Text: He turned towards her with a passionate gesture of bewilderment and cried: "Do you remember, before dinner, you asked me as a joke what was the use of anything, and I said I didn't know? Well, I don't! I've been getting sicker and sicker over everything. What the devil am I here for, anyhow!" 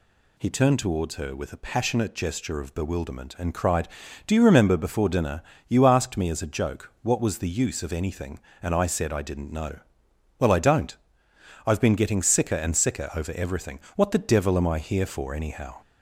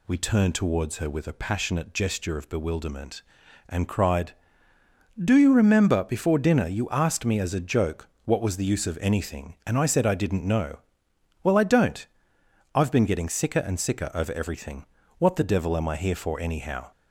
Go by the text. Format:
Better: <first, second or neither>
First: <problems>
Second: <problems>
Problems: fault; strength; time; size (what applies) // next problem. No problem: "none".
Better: first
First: none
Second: says "We" for "He"; at 0.0 s // pauses between "joke" and "what"; slight; at 8.0 s; 0.18 s long